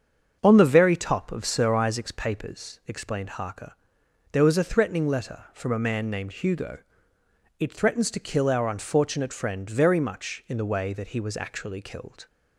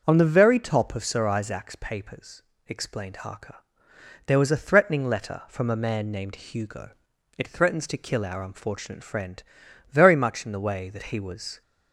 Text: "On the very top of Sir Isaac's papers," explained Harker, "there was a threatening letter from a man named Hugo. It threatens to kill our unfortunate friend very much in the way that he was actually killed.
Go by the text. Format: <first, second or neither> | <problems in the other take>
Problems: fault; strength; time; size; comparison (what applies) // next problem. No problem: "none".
first | starts louder than the rest; until 1.0 s; 6.5 dB; also in the first // pauses between "friend" and "very"; noticeable; at 9.4 s; 0.50 s long // stops before "actually killed"; at 11.6 s